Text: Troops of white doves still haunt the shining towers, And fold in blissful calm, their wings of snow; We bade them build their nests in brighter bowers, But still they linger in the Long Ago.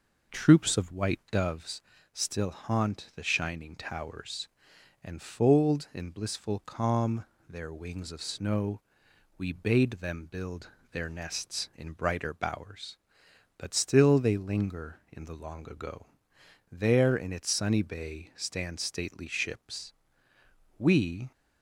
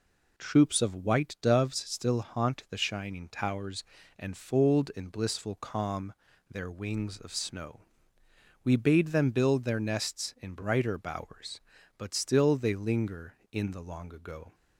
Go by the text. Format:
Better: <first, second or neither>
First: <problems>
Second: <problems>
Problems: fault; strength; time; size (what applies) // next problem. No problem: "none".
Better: second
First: pauses between "doves" and "still"; slight; at 1.8 s; 0.32 s long // pauses between "build" and "their"; slight; at 10.6 s; 0.22 s long // goes on to say "There in its sunny bay stand stately ships We"; strong; from 16.7 s on; 4.6 s long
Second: none